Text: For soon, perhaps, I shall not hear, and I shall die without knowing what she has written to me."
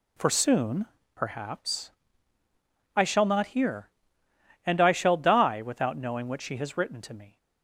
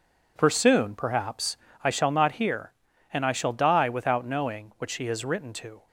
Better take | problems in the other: first | stops before "me"; at 5.8 s

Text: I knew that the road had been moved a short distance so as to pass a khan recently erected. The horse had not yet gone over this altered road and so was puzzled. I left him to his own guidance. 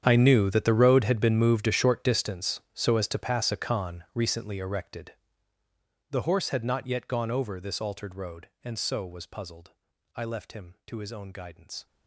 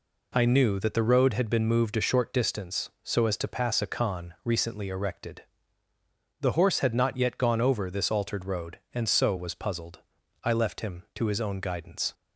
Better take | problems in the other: second | gets quieter; strong; throughout; 18 dB

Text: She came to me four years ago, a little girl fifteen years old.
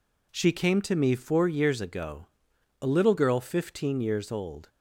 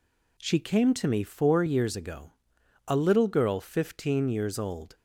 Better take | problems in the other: neither | none

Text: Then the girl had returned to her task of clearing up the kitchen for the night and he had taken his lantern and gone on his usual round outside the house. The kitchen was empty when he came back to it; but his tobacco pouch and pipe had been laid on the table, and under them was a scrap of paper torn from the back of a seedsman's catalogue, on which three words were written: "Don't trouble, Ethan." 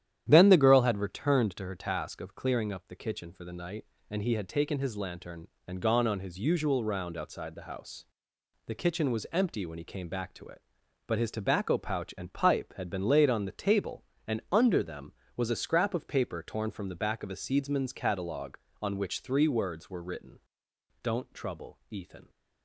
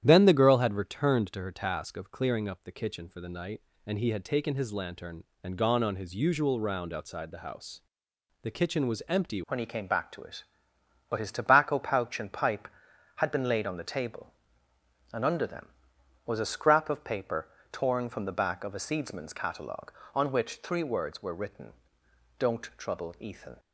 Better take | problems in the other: first | starts louder than the rest; strong; until 1.0 s; 10.5 dB; strong in the first // changes voice at "when"; from 9.4 s on; 14.1 s long // pauses between "paper" and "torn"; slight; at 17.4 s; 0.26 s long

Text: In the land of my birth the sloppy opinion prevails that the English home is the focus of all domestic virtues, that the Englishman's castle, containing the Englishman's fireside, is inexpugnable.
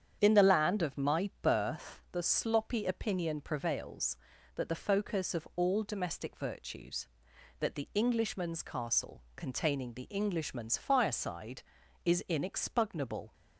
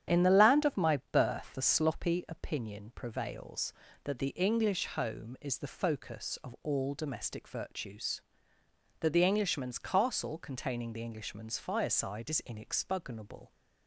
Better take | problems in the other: second | starts louder than the rest; strong; until 1.2 s; 8.5 dB; strong in the second // skips "the English home is"; at 4.6 s

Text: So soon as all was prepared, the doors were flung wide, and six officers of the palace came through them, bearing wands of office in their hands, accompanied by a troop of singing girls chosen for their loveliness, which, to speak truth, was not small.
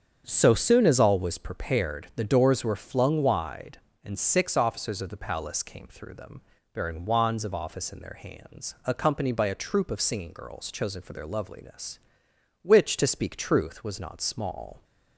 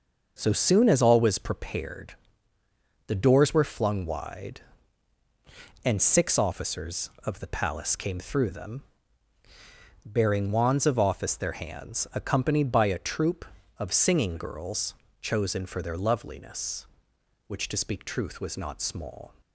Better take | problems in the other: first | starts louder than the rest; noticeable; until 1.4 s; 6 dB; strong in the first // skips "in"; at 11.3 s // pauses between "girls" and "chosen"; slight; at 14.9 s; 0.28 s long

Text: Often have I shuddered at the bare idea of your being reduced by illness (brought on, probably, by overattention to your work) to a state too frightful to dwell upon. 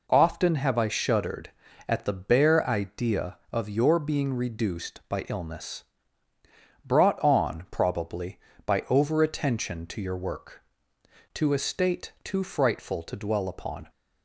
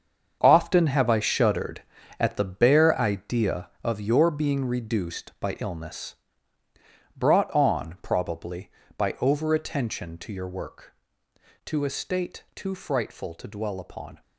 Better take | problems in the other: first | gets quieter; strong; throughout; 11 dB

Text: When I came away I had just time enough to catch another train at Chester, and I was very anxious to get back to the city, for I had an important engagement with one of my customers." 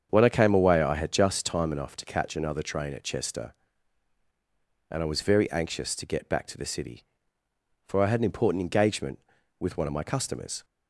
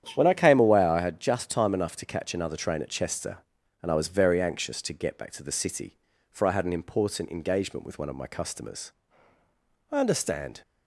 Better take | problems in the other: first | starts louder than the rest; strong; until 1.1 s; 9.5 dB; strong in the first // goes on to say "I understand"; noticeable; from 9.9 s on; 0.70 s long

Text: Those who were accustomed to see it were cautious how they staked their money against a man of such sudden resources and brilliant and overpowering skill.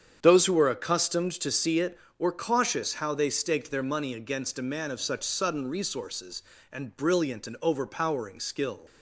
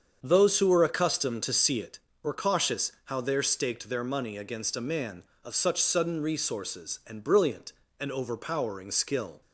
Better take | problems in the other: first | starts louder than the rest; until 1.2 s; 7 dB; strong in the first // says "there" for "they"; at 3.2 s

